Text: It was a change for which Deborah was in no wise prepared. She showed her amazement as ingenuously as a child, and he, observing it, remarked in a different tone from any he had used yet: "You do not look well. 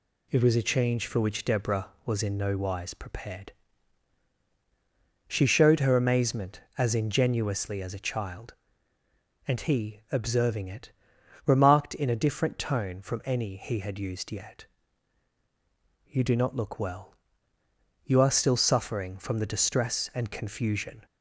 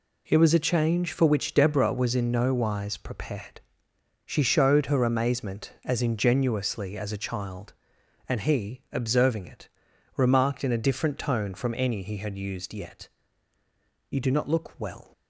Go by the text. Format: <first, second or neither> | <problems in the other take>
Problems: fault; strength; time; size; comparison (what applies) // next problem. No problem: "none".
second | goes on to say "You are still suffering from the distress and confusion"; strong; from 18.0 s on; 3.0 s long